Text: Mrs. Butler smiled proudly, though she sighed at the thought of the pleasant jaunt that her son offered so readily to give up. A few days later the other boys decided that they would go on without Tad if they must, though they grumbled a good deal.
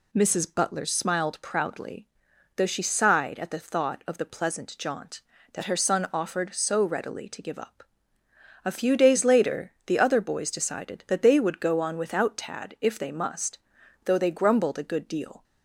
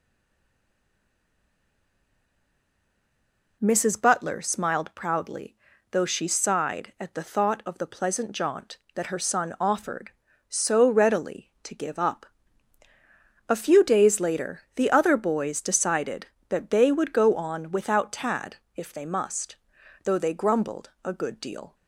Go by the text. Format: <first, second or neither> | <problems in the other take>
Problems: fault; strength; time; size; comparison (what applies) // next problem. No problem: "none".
first | stays silent before the first word; strong; until 3.6 s; 3.6 s long // pauses between "Tad" and "if"; slight; at 18.5 s; 0.20 s long